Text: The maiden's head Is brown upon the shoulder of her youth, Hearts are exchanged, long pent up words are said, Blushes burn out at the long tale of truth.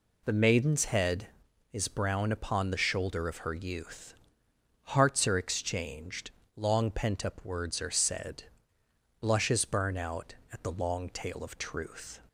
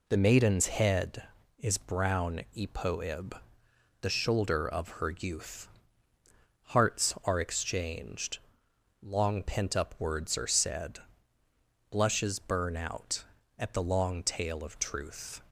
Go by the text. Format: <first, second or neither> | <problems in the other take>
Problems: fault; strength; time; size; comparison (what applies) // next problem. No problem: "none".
first | says "epoib" for "upon"; at 2.5 s